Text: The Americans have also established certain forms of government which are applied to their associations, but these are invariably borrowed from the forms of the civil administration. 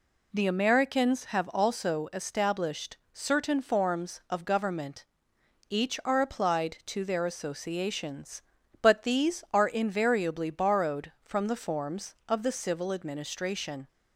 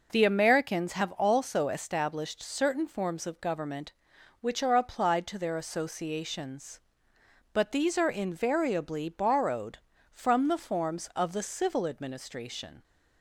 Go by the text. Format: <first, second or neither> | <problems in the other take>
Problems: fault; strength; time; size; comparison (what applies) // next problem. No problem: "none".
second | pauses between "established" and "certain"; slight; at 2.9 s; 0.16 s long // says "each" for "which"; at 5.6 s